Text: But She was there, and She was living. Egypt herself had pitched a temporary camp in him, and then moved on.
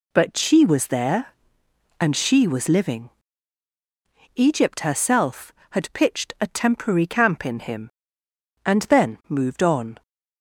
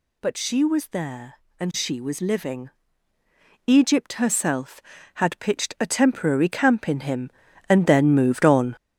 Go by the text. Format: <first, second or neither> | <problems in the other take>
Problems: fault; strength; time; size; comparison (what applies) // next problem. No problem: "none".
first | gets louder; strong; throughout; 7 dB